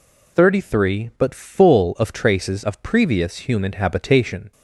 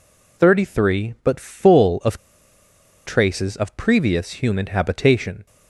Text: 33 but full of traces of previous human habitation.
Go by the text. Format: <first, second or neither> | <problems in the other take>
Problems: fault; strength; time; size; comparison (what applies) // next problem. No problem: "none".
first | pauses between "of" and "traces"; noticeable; at 2.1 s; 0.89 s long